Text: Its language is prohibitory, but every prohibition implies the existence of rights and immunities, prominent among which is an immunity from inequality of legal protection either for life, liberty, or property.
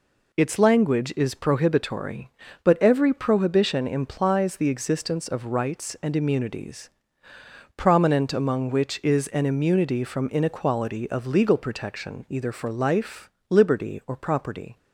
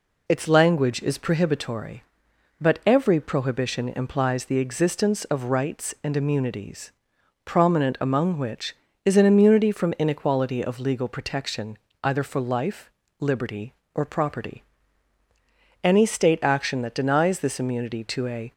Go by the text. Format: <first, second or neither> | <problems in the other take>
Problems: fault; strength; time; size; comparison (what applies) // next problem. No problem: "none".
first | pauses between "protection" and "either"; slight; at 11.7 s; 0.24 s long // goes on to say "Any State action that denies this immunity to a"; strong; from 15.8 s on; 2.7 s long